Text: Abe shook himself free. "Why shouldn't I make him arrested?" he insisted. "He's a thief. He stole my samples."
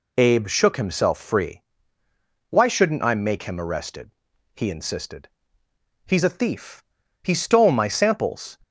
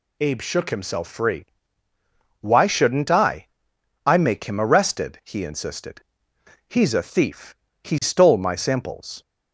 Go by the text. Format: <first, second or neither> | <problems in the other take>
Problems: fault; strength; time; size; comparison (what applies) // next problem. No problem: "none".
first | says "I" twice; at 4.0 s